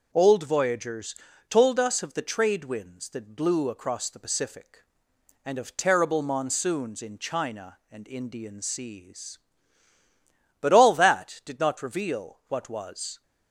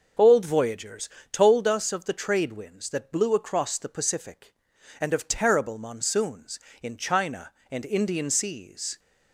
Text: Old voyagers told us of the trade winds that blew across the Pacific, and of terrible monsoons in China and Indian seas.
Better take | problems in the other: second | pauses between "voyagers" and "told"; slight; at 1.1 s; 0.32 s long; slight in the second // goes on to say "But all that did not reveal what was"; strong; from 10.5 s on; 2.6 s long

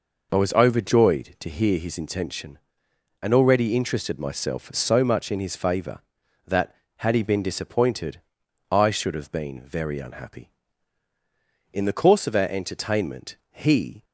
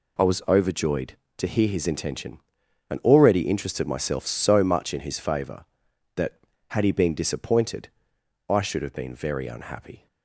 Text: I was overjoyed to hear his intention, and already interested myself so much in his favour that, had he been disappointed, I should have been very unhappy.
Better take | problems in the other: second | goes on to say "In the course of our entertainment he"; strong; from 11.7 s on; 2.3 s long

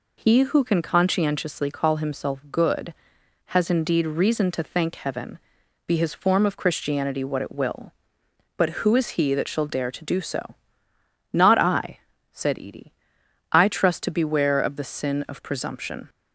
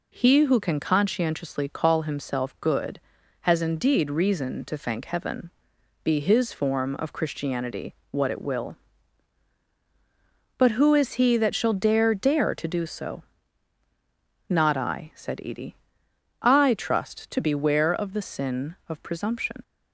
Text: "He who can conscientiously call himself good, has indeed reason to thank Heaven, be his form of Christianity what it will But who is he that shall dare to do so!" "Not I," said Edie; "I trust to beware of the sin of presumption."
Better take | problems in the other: first | pauses between "Christianity" and "what"; slight; at 7.9 s; 0.16 s long // says "dare" twice; at 12.1 s

